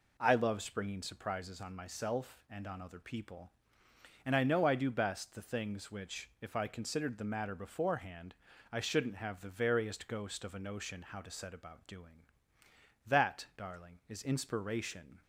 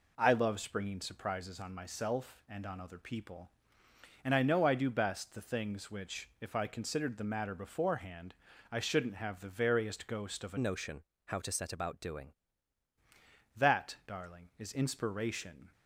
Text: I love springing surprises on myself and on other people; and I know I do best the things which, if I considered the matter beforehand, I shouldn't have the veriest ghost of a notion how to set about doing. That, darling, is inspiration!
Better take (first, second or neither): first